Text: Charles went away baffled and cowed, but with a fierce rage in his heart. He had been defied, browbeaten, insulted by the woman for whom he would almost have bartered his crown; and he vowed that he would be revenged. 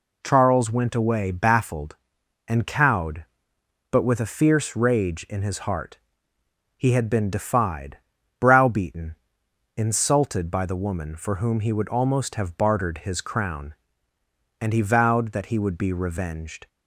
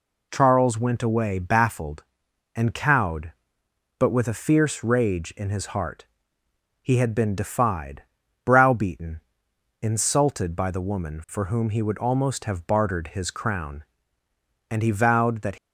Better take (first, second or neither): first